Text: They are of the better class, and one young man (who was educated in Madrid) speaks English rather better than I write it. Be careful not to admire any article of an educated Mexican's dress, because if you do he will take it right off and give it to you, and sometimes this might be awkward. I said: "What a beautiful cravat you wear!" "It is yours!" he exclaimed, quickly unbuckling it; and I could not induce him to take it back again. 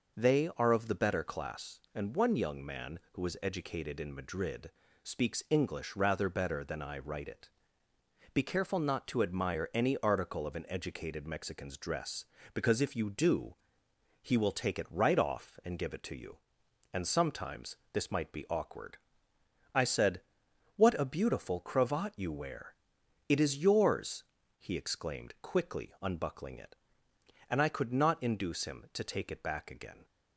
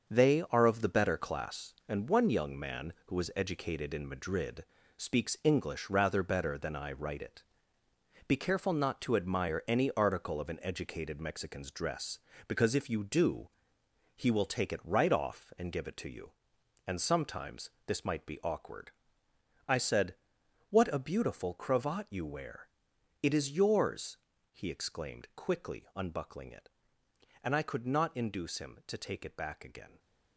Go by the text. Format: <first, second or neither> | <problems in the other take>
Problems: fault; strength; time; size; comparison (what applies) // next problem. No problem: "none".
first | gets quieter; strong; throughout; 8 dB // pauses between "do" and "he"; noticeable; at 13.4 s; 0.68 s long; noticeable in the first // pauses between "sometimes" and "this"; slight; at 17.6 s; 0.18 s long; slight in the first